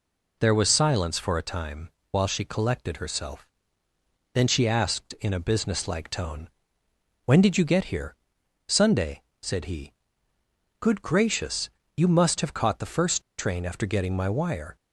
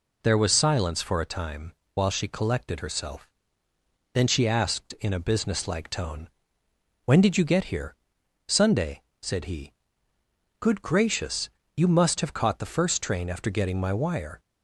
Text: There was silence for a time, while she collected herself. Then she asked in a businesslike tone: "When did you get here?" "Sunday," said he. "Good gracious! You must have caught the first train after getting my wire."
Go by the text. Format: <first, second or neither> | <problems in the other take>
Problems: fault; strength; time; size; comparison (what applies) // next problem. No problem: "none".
second | pauses between "first" and "train"; slight; at 13.2 s; 0.16 s long